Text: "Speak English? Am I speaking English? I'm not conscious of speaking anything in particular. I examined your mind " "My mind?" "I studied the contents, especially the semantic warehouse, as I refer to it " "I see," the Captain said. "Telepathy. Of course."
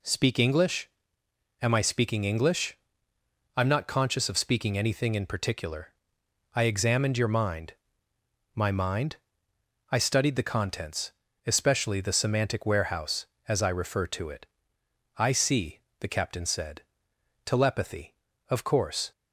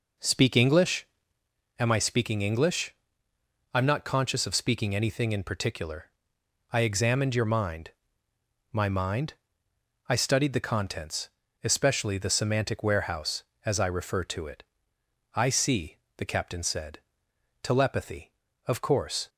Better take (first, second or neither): first